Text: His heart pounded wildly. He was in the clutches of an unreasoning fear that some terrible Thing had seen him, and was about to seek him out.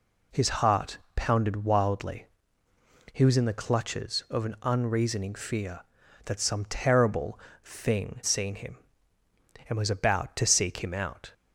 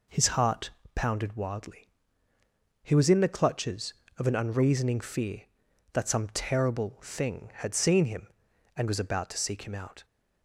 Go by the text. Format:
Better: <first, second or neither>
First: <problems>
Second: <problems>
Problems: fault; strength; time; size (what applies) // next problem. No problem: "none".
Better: second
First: pauses between "heart" and "pounded"; slight; at 0.9 s; 0.16 s long // pauses between "terrible" and "Thing"; slight; at 7.3 s; 0.26 s long // skips "had"; at 8.2 s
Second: pauses between "heart" and "pounded"; slight; at 0.7 s; 0.24 s long